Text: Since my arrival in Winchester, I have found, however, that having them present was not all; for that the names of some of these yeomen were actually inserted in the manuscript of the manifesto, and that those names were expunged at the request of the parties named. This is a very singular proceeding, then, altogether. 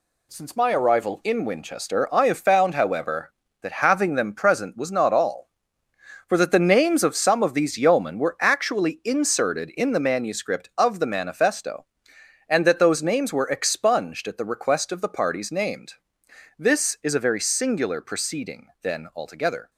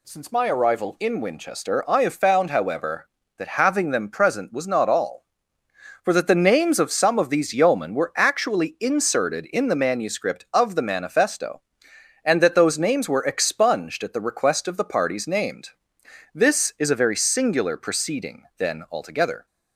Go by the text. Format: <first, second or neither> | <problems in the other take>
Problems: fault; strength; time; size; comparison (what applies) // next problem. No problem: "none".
second | gets quieter; noticeable; throughout; 5.5 dB